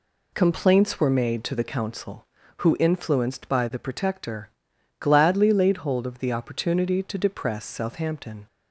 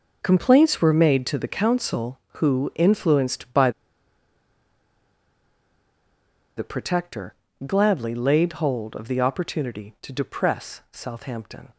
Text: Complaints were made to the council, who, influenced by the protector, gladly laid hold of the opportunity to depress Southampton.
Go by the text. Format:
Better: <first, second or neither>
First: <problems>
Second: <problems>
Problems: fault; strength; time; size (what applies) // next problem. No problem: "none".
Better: first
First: none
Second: pauses between "by" and "the"; strong; at 3.7 s; 2.8 s long